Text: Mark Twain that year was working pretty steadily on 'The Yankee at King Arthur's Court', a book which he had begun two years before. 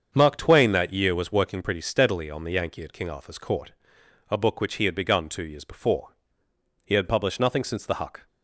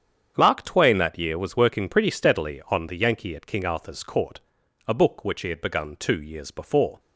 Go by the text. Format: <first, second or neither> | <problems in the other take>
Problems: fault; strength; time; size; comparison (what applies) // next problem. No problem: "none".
second | starts louder than the rest; until 1.1 s; 7 dB; strong in the second // goes on to say "He had published nothing since the Huck"; from 6.8 s on; 1.4 s long